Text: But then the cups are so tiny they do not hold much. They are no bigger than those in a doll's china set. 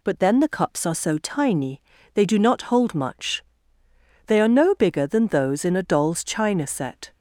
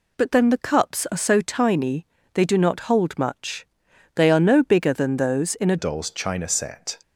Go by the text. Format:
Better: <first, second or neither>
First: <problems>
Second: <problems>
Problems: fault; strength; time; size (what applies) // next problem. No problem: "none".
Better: first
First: pauses between "tiny" and "they"; slight; at 1.8 s; 0.32 s long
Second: pauses between "tiny" and "they"; slight; at 2.0 s; 0.28 s long // changes voice at "doll's"; from 5.7 s on; 1.3 s long